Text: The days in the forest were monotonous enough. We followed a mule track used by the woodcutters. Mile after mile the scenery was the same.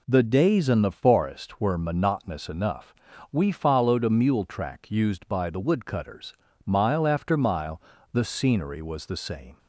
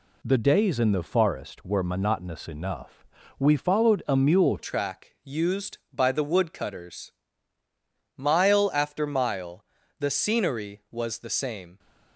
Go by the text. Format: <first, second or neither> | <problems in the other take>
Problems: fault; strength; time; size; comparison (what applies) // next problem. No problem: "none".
first | changes voice at "track"; from 4.5 s on; 7.2 s long // pauses between "mile" and "the"; slight; at 9.6 s; 0.34 s long; slight in the first